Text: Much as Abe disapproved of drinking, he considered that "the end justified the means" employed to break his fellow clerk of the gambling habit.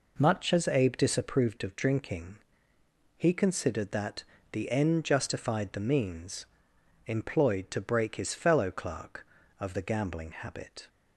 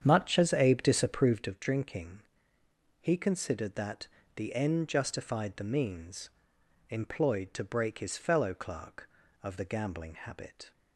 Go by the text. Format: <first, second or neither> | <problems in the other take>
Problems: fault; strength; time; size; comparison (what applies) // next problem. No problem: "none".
first | starts louder than the rest; strong; until 1.6 s; 8.5 dB // pauses between "that" and "the"; slight; at 4.0 s; 0.26 s long; slight in the first // pauses between "means" and "employed"; noticeable; at 6.2 s; 0.61 s long; noticeable in the first